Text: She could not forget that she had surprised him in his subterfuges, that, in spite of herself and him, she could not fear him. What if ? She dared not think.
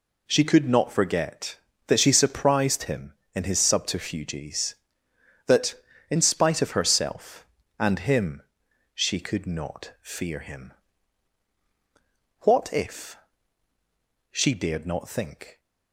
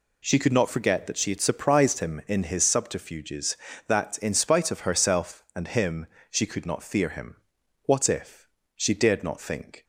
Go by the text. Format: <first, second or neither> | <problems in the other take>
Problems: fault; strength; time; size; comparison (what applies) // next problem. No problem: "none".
second | skips "had"; at 2.1 s